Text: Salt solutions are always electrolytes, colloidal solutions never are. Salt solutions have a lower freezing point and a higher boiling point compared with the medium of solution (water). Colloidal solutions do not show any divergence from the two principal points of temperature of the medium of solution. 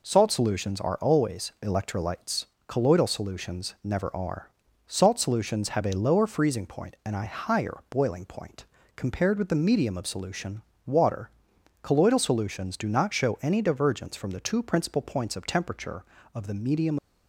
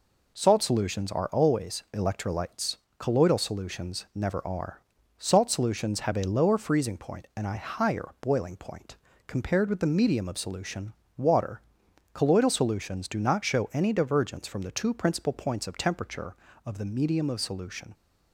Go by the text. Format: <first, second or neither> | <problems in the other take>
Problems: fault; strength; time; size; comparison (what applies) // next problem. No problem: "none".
second | pauses between "point" and "compared"; slight; at 8.6 s; 0.32 s long; slight in the second // stops before "of solution"; at 16.9 s